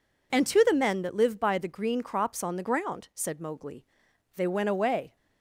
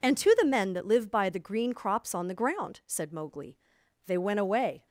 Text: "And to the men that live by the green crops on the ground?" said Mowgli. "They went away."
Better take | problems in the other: neither | none

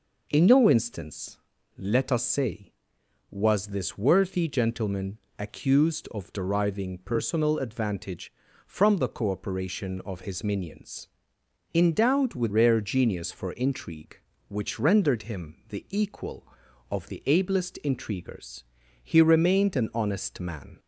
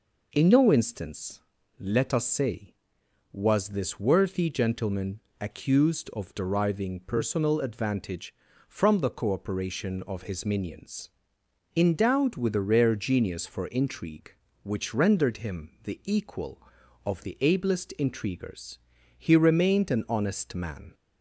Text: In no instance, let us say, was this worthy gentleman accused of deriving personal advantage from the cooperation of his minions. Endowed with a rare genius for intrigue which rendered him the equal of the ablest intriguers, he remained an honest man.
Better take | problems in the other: second | pauses between "gentleman" and "accused"; slight; at 5.1 s; 0.22 s long; slight in the second // skips "a"; at 12.5 s

